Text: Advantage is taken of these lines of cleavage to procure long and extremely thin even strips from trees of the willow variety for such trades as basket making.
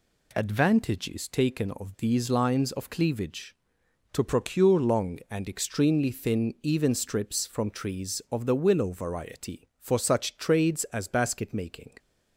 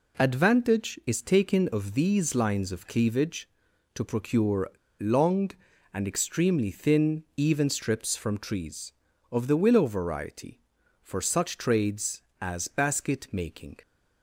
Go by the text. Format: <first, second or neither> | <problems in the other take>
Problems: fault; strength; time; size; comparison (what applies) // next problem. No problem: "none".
first | pauses between "procure" and "long"; slight; at 4.6 s; 0.30 s long // pauses between "thin" and "even"; slight; at 7.2 s; 0.16 s long